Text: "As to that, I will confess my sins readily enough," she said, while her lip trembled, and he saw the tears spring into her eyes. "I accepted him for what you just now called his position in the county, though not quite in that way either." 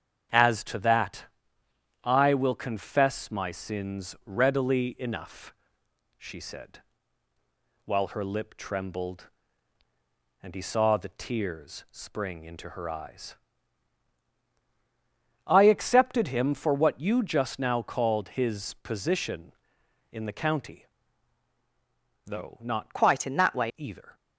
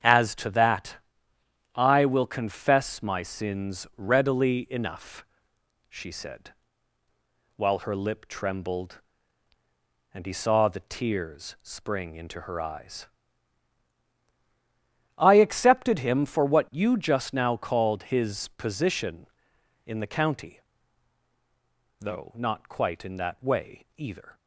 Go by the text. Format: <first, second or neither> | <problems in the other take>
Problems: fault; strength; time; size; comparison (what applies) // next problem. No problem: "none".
second | starts louder than the rest; strong; until 2.1 s; 8 dB; strong in the second // changes voice from "quite" to "way"; from 22.9 to 23.7 s; 0.8 s long